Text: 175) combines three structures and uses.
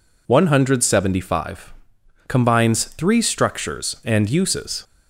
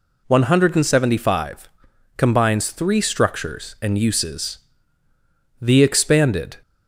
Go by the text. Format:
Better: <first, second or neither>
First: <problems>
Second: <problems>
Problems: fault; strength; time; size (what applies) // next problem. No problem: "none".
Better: first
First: none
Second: goes on to say "The expanded"; noticeable; from 5.5 s on; 0.98 s long